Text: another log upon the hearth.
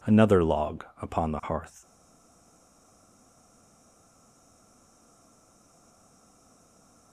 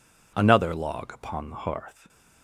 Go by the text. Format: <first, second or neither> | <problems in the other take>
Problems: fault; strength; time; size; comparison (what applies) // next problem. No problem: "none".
second | pauses between "log" and "upon"; slight; at 0.8 s; 0.16 s long // stays silent after the last word; strong; from 1.8 s on; 5.3 s long